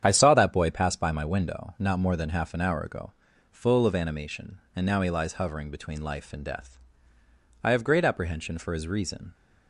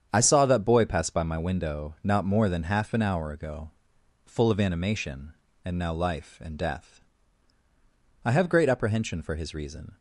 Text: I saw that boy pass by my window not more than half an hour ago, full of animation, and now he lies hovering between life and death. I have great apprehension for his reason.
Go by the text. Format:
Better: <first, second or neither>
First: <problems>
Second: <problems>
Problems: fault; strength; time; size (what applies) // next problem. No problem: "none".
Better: first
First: starts louder than the rest; strong; until 1.0 s; 8.5 dB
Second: starts louder than the rest; strong; until 1.1 s; 8 dB // skips "he lies hovering between"; at 5.9 s